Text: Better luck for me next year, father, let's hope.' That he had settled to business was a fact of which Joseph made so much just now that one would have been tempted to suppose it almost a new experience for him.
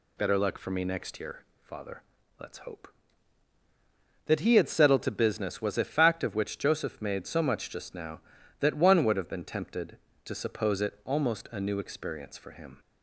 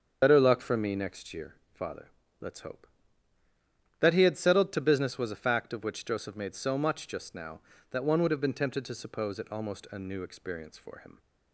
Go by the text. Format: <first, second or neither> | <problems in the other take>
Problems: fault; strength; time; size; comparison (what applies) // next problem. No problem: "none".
first | loses the start of "Better"; at 0.2 s; 60 ms // starts louder than the rest; until 1.2 s; 7 dB